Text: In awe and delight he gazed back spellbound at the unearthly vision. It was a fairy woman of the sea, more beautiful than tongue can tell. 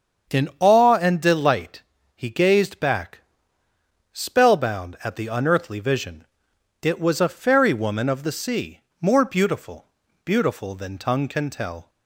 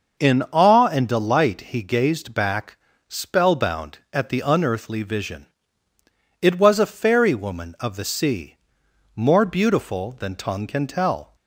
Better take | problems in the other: second | starts louder than the rest; until 1.4 s; 7 dB // pauses between "delight" and "he"; slight; at 1.8 s; 0.30 s long // pauses between "back" and "spellbound"; noticeable; at 3.1 s; 0.92 s long; slight in the second // says "beautiful" twice; at 10.2 s

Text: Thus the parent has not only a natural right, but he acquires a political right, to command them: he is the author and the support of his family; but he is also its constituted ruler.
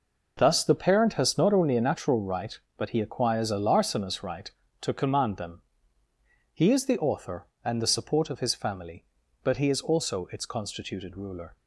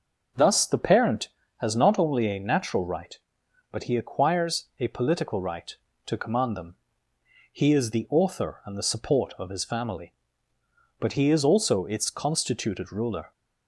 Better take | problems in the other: second | says "larcenous" for "political"; at 3.5 s

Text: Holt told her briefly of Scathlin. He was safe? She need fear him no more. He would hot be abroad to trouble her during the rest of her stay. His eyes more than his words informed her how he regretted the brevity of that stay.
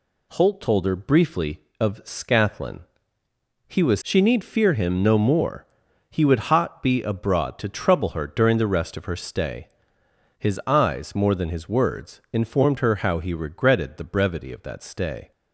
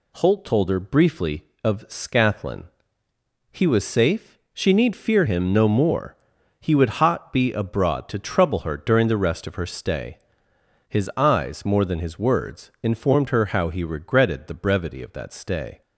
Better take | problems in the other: second | skips "safe"; at 4.0 s

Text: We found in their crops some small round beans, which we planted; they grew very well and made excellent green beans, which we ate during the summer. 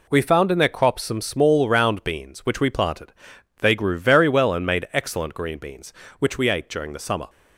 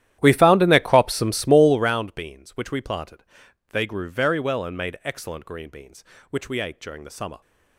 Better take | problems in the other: first | starts louder than the rest; strong; until 2.0 s; 12 dB

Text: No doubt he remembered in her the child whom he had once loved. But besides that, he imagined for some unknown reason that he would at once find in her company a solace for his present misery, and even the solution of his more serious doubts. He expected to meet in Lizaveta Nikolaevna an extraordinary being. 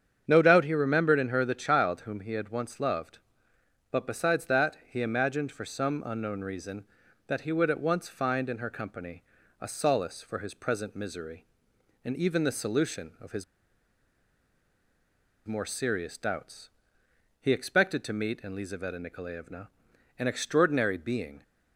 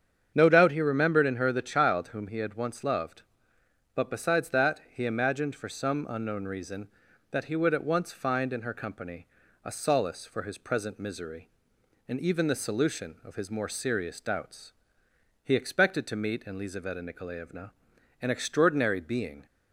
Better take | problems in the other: second | starts louder than the rest; strong; until 1.2 s; 8 dB; strong in the second // pauses between "company" and "a"; at 9.2 s; 0.38 s long; also in the second // pauses between "his" and "more"; strong; at 13.4 s; 2.0 s long // pauses between "Nikolaevna" and "an"; noticeable; at 19.6 s; 0.50 s long; noticeable in the second

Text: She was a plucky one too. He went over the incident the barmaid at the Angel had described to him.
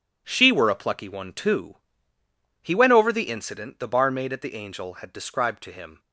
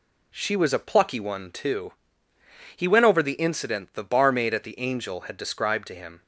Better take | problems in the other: second | says "were" for "was"; at 0.4 s

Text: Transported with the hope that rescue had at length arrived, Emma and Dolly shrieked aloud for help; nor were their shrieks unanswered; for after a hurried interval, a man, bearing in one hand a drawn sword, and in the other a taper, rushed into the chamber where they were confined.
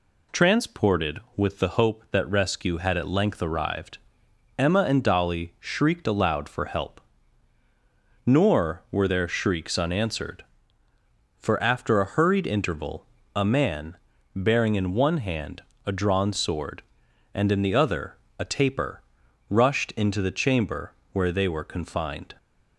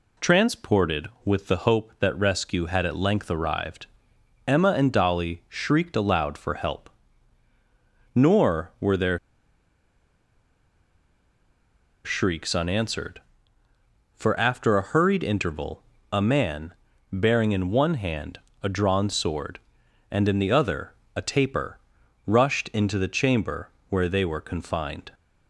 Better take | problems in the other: first | pauses between "their" and "shrieks"; strong; at 9.1 s; 2.8 s long // pauses between "hand" and "a"; slight; at 18.3 s; 0.24 s long; slight in the first // pauses between "other" and "a"; slight; at 20.9 s; 0.20 s long; slight in the first // pauses between "chamber" and "where"; slight; at 23.6 s; 0.20 s long; slight in the first

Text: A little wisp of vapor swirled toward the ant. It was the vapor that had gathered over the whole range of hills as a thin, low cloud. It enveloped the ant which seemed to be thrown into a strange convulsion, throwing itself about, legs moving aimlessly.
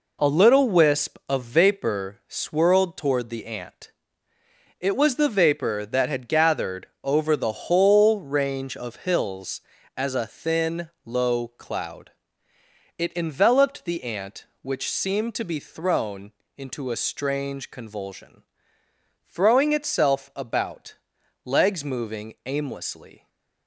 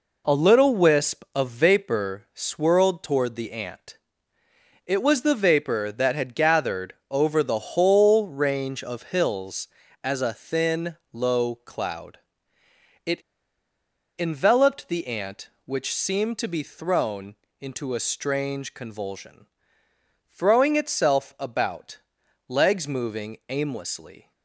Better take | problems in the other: first | pauses between "gathered" and "over"; slight; at 6.9 s; 0.18 s long; slight in the first // pauses between "It" and "enveloped"; noticeable; at 13.2 s; 0.97 s long // pauses between "thrown" and "into"; slight; at 17.3 s; 0.24 s long; slight in the first

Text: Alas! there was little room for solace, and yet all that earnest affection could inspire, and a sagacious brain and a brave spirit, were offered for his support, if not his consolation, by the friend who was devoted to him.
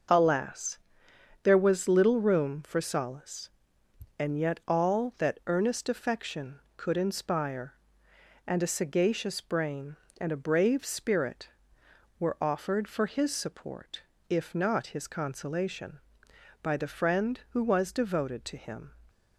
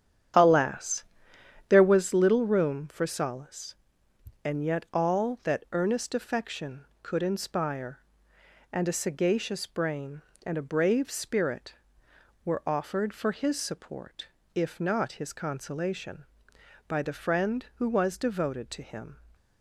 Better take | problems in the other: first | starts louder than the rest; strong; until 2.2 s; 9 dB

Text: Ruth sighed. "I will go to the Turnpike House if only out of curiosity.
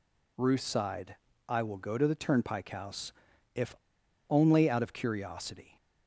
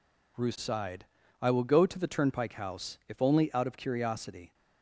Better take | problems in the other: second | pauses between "House" and "if"; noticeable; at 3.1 s; 0.46 s long // pauses between "if" and "only"; noticeable; at 3.7 s; 0.55 s long

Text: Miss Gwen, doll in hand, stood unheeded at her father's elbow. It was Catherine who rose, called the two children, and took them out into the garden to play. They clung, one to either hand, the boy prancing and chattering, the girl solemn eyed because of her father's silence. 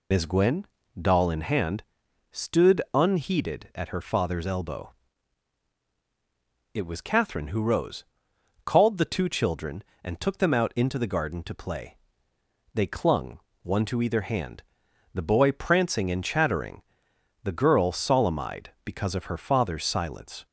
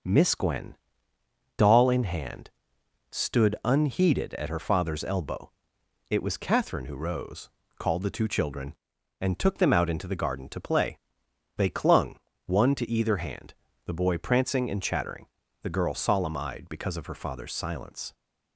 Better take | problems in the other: second | loses the start of "Miss"; at 0.1 s; 75 ms

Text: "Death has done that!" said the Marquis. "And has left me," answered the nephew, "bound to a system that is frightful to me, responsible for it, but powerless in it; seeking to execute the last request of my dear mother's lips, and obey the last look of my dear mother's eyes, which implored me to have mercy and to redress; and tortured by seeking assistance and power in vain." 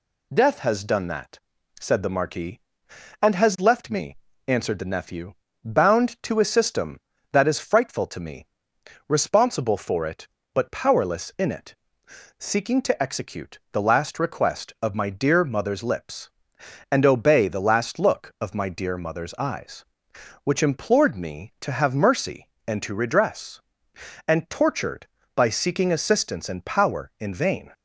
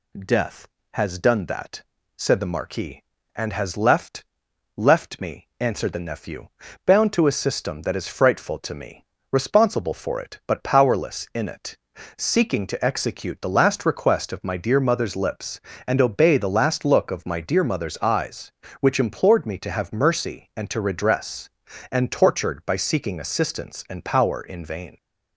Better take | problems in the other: first | says "left" twice; at 4.7 s

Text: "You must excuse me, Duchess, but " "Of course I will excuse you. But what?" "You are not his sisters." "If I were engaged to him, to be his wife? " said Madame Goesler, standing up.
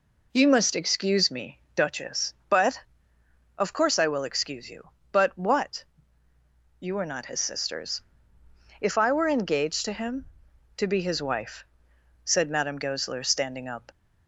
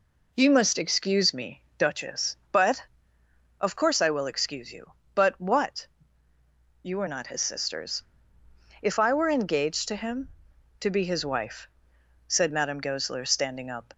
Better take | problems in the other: neither | none

